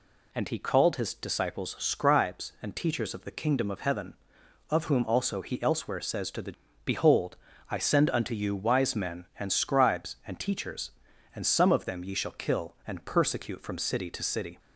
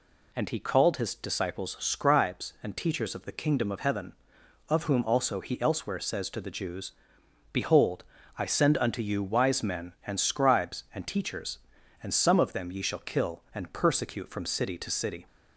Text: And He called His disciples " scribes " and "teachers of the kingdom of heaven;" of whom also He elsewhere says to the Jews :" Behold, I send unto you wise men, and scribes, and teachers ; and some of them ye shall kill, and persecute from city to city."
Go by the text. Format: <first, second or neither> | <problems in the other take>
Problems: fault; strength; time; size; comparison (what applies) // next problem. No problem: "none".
second | skips "Jews"; at 6.5 s